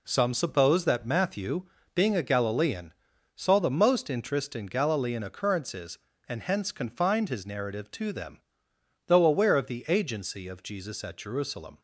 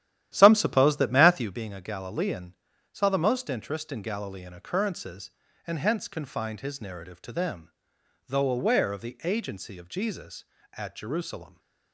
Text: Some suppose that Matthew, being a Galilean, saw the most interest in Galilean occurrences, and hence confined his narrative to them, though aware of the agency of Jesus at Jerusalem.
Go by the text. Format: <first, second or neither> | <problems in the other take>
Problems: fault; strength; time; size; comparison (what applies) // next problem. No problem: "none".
first | starts louder than the rest; strong; until 1.6 s; 12 dB